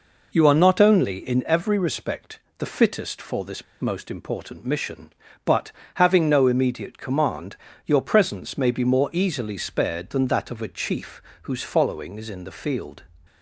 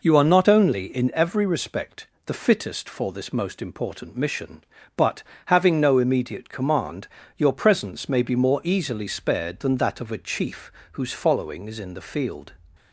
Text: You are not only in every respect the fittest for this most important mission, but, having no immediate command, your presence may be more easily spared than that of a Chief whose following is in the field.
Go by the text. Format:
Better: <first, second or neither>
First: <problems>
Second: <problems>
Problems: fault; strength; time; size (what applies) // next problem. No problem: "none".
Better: second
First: pauses between "respect" and "the"; slight; at 2.3 s; 0.18 s long // pauses between "this" and "most"; slight; at 3.6 s; 0.18 s long // pauses between "Chief" and "whose"; slight; at 11.1 s; 0.22 s long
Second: pauses between "respect" and "the"; slight; at 2.0 s; 0.18 s long // pauses between "Chief" and "whose"; slight; at 10.6 s; 0.22 s long